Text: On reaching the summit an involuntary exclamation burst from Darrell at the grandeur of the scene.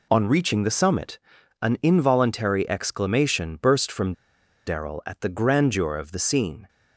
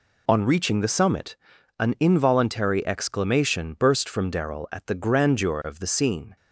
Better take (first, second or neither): second